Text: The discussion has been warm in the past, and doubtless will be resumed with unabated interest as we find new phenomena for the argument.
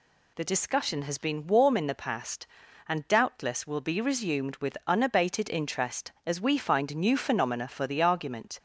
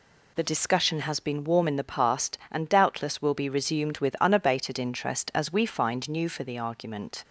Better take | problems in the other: first | skips "phenomena"; at 6.2 s

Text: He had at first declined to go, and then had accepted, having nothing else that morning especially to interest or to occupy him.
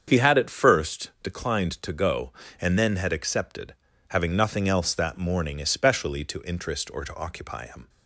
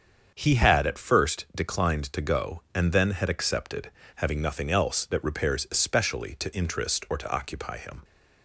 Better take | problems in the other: first | starts louder than the rest; until 1.3 s; 7 dB; strong in the first // says "repairs" for "morning"; at 5.2 s

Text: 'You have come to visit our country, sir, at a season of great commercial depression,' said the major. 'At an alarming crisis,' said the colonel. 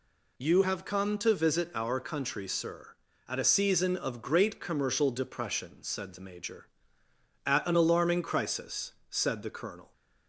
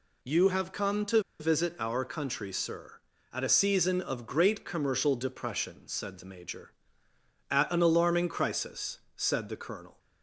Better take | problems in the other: first | pauses between "to" and "visit"; slight; at 1.1 s; 0.20 s long

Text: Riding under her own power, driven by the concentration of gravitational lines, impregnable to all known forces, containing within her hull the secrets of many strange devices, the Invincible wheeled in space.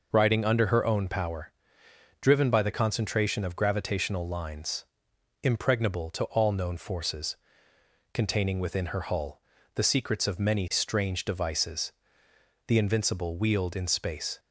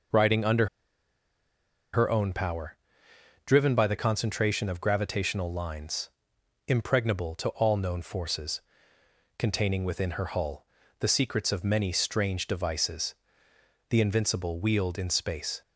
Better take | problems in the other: first | pauses between "under" and "her"; strong; at 0.6 s; 1.2 s long // pauses between "hull" and "the"; slight; at 10.6 s; 0.34 s long; slight in the first

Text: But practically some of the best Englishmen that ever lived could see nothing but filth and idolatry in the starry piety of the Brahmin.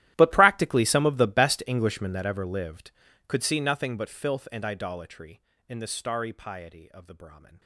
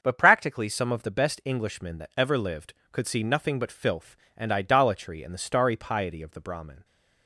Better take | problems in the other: second | gets quieter; strong; throughout; 21.5 dB // starts louder than the rest; strong; until 1.1 s; 13.5 dB; also in the second

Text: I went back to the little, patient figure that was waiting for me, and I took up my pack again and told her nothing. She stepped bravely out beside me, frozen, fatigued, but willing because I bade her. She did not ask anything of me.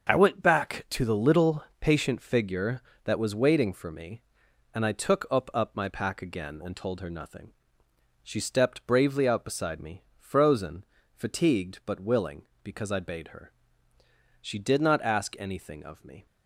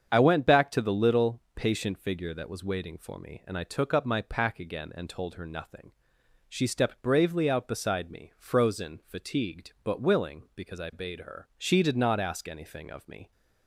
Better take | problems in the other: second | starts louder than the rest; until 1.1 s; 6.5 dB; strong in the second // says "up" twice; at 5.5 s

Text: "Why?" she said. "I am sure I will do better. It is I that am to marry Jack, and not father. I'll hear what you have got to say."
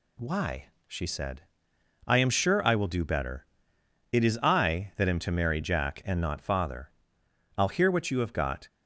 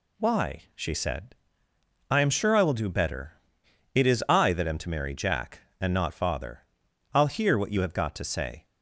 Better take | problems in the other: second | stops before "to say"; at 8.6 s

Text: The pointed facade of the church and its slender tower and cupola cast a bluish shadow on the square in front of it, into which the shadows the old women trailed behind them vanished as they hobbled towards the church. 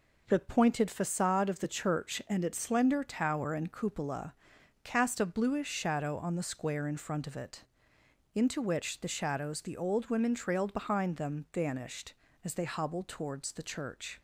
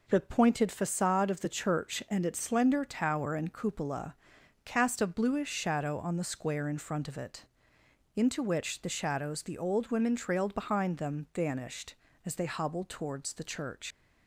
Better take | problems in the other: first | pauses between "cupola" and "cast"; noticeable; at 4.1 s; 0.48 s long; noticeable in the first // leaves "church" unfinished; at 13.9 s; 100 ms

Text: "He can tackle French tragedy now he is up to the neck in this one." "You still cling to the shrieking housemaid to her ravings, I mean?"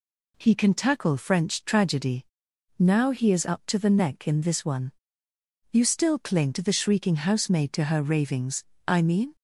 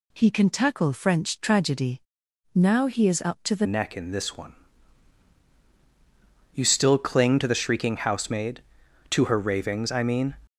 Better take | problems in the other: first | pauses between "tragedy" and "now"; noticeable; at 2.0 s; 0.52 s long; noticeable in the first // changes voice at "neck"; from 3.6 s on; 6.7 s long

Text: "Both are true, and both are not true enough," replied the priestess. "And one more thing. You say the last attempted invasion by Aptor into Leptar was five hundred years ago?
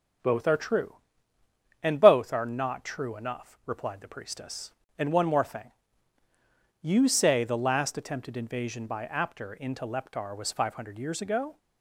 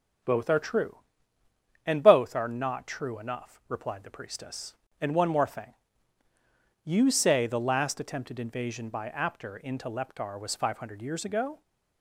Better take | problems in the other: neither | starts louder than the rest; the same in both

